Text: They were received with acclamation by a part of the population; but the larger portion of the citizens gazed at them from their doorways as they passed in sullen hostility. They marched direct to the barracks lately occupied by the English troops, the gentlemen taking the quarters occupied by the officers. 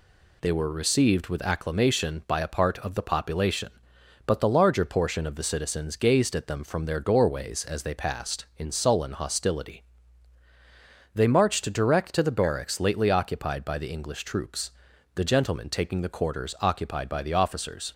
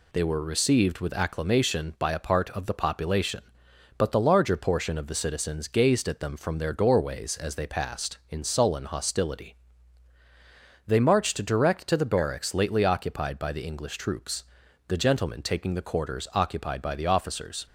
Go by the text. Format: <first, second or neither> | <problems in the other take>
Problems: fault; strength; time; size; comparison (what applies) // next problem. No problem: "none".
neither | none